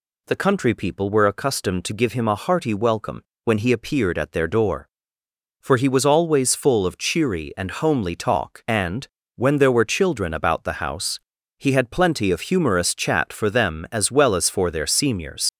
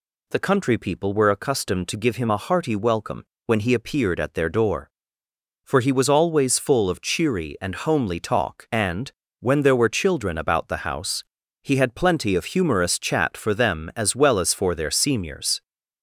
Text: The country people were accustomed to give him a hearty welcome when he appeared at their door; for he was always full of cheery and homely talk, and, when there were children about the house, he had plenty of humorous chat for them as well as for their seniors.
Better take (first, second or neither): second